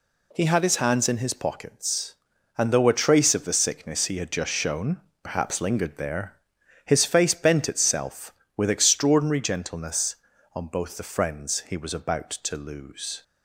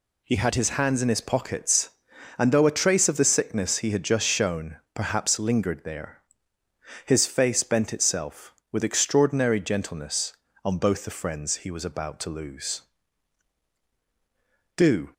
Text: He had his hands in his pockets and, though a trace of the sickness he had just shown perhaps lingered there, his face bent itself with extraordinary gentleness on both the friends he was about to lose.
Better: first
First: pauses between "shown" and "perhaps"; slight; at 4.9 s; 0.24 s long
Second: pauses between "shown" and "perhaps"; slight; at 4.7 s; 0.18 s long // goes on to say "Do"; slight; from 14.7 s on; 0.36 s long

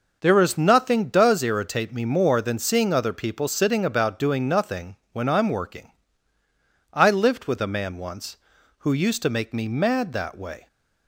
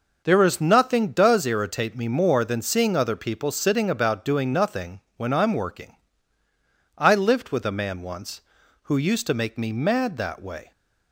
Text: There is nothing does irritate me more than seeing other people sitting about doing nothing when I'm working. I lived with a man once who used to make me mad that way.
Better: neither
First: none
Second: none

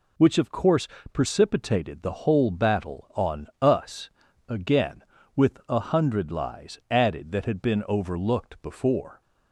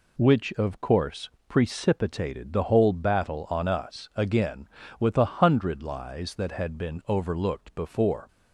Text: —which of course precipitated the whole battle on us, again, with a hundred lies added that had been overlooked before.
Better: first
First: pauses between "course" and "precipitated"; slight; at 0.8 s; 0.26 s long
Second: pauses between "course" and "precipitated"; slight; at 1.2 s; 0.18 s long // skips "added"; at 6.3 s

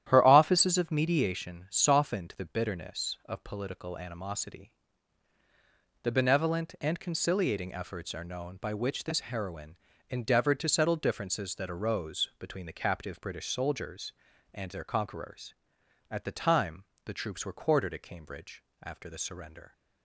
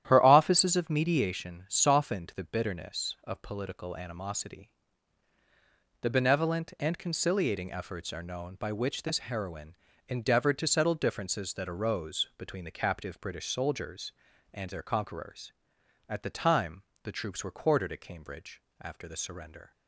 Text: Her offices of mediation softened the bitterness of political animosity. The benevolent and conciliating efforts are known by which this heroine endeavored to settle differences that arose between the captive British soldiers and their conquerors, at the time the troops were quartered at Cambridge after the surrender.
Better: neither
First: starts louder than the rest; strong; until 1.0 s; 11.5 dB // pauses between "heroine" and "endeavored"; slight; at 9.7 s; 0.32 s long // pauses between "time" and "the"; slight; at 16.8 s; 0.20 s long // pauses between "Cambridge" and "after"; slight; at 18.6 s; 0.22 s long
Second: starts louder than the rest; strong; until 1.0 s; 11.5 dB // pauses between "heroine" and "endeavored"; slight; at 9.7 s; 0.32 s long // pauses between "time" and "the"; slight; at 16.8 s; 0.20 s long // pauses between "Cambridge" and "after"; slight; at 18.6 s; 0.22 s long

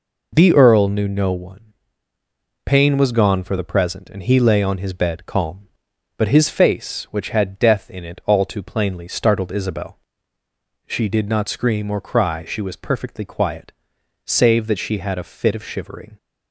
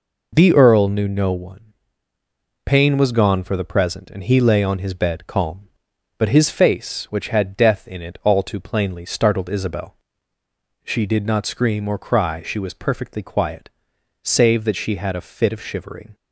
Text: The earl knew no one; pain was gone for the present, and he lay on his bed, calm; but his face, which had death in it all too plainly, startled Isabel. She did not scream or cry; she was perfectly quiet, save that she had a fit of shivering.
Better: neither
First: none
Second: none

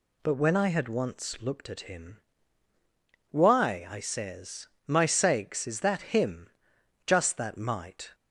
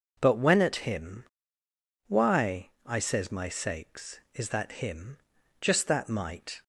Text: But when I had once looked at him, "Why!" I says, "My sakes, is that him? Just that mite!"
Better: first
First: none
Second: skips "I had once looked"; at 0.6 s

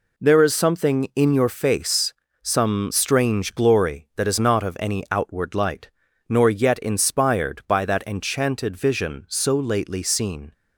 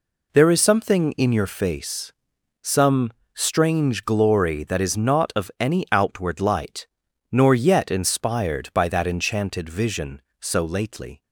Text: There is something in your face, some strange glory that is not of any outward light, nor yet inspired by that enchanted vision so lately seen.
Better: first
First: none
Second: pauses between "some" and "strange"; slight; at 3.0 s; 0.24 s long // stops before "seen"; at 11.2 s

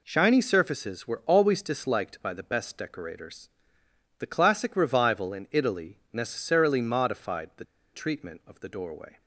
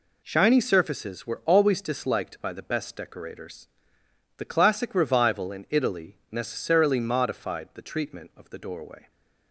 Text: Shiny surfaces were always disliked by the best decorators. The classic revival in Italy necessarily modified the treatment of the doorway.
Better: second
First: pauses between "the" and "treatment"; slight; at 7.6 s; 0.28 s long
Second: none

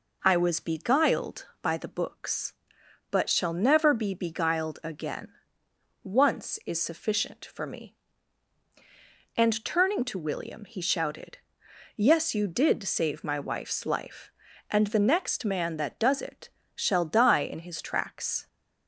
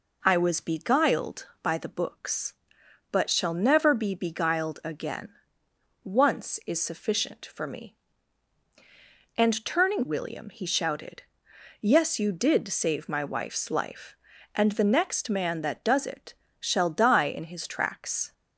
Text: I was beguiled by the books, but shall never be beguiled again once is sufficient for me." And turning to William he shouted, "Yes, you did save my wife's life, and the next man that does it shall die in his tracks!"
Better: first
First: pauses between "again" and "once"; noticeable; at 5.2 s; 0.76 s long // pauses between "it" and "shall"; slight; at 16.4 s; 0.26 s long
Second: pauses between "again" and "once"; noticeable; at 5.2 s; 0.76 s long // skips "to"; at 10.0 s // pauses between "it" and "shall"; slight; at 16.3 s; 0.26 s long

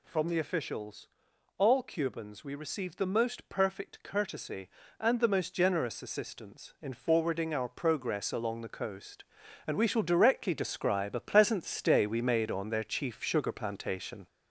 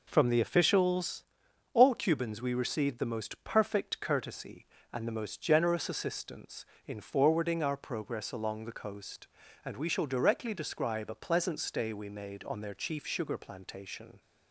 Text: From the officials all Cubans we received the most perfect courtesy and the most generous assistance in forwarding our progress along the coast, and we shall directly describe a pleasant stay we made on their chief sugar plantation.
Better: second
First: gets louder; noticeable; throughout; 4.5 dB // pauses between "officials" and "all"; noticeable; at 1.0 s; 0.50 s long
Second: pauses between "officials" and "all"; noticeable; at 1.2 s; 0.52 s long

